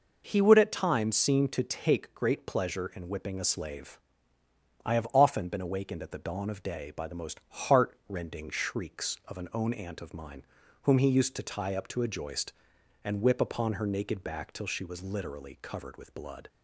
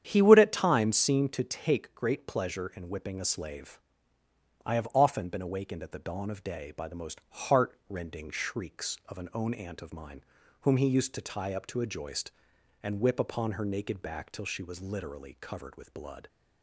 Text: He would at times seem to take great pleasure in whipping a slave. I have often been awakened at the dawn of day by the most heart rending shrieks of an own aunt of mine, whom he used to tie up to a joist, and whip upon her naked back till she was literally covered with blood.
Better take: first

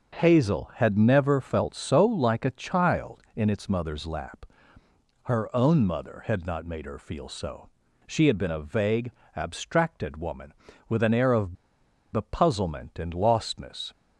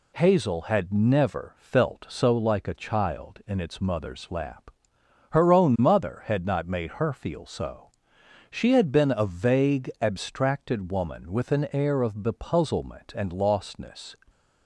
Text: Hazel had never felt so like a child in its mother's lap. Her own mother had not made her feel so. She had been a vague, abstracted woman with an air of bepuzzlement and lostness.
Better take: second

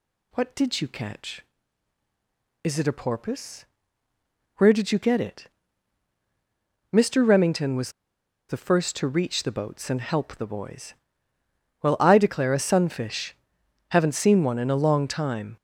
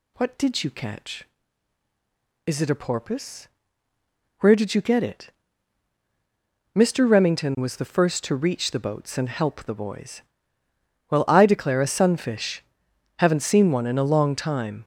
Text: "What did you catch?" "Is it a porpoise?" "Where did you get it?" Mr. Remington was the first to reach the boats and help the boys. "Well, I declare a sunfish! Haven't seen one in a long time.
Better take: second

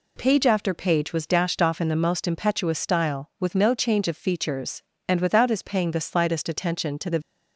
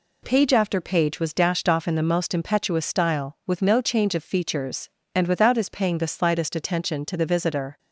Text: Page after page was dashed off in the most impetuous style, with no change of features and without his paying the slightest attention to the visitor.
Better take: second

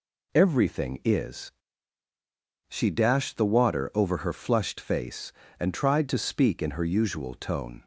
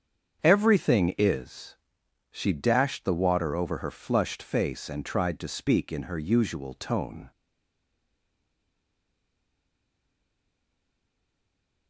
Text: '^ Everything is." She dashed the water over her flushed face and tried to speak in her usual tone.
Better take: first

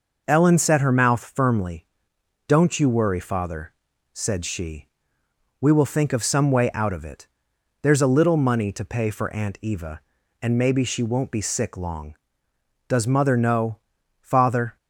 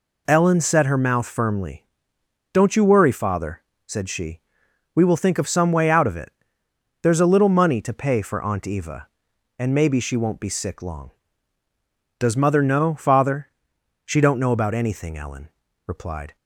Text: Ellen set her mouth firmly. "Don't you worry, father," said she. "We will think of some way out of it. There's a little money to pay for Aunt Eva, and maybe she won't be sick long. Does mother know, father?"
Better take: first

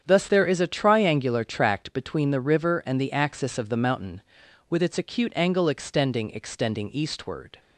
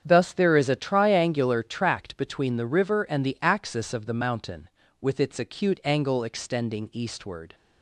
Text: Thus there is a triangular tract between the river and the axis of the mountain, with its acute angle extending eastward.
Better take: second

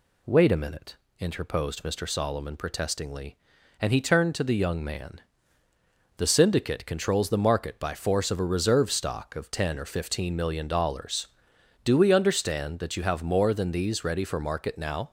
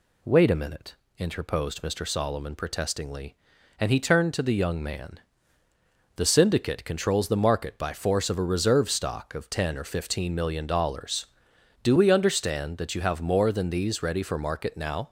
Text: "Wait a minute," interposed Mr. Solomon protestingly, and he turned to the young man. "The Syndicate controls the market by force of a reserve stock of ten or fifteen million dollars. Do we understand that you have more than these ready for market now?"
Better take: neither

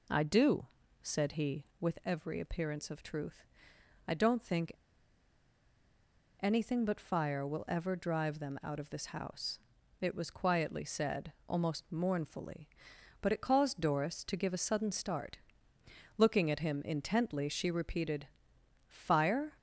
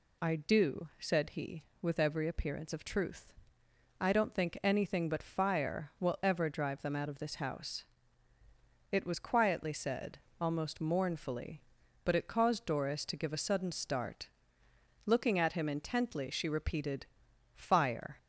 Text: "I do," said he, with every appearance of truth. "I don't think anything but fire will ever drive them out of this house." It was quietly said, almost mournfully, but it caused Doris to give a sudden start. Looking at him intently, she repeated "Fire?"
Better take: second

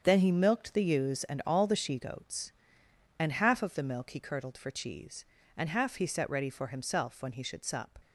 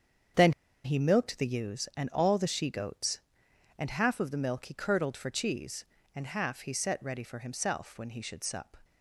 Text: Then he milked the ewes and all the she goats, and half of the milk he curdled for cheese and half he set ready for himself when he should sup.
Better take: first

